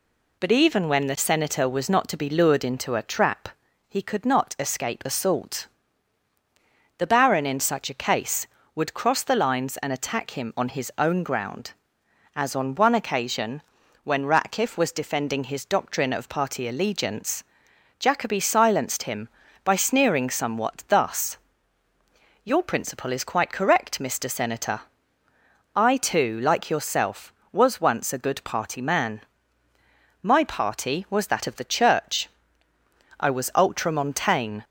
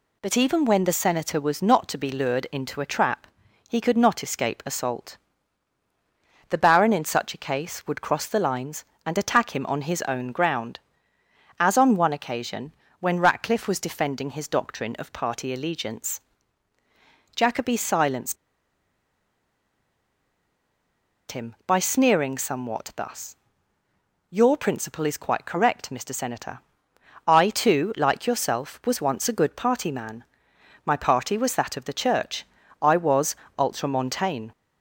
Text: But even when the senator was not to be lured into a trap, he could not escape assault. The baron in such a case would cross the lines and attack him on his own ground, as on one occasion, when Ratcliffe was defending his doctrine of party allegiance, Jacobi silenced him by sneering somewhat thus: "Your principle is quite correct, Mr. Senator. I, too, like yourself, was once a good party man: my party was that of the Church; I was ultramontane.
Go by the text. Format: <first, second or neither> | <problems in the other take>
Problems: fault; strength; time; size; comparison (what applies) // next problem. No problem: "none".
first | pauses between "silenced" and "him"; strong; at 18.3 s; 2.9 s long // pauses between "was" and "ultramontane"; slight; at 33.3 s; 0.22 s long